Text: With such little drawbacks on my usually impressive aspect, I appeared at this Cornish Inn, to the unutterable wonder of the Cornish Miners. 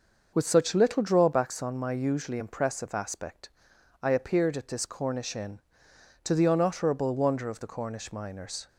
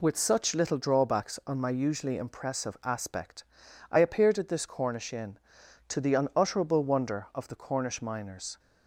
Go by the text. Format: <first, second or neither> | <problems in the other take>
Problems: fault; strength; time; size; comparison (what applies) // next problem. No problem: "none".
neither | none